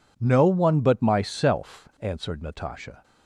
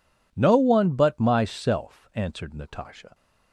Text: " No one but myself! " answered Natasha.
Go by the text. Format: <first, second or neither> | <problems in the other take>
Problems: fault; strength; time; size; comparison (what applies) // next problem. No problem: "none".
neither | none